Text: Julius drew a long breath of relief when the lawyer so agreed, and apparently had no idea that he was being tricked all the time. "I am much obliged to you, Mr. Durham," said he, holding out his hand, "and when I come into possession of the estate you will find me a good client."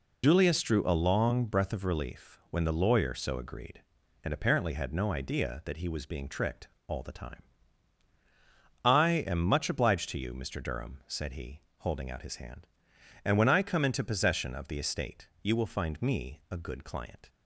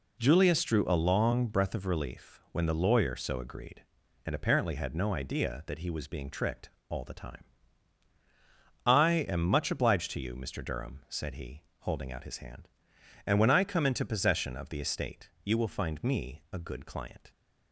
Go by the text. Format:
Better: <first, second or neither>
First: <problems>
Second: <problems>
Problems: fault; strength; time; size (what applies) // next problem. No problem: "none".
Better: second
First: loses the start of "Julius"; at 0.2 s; 70 ms // pauses between "tricked" and "all"; slight; at 6.6 s; 0.18 s long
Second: pauses between "tricked" and "all"; slight; at 6.7 s; 0.18 s long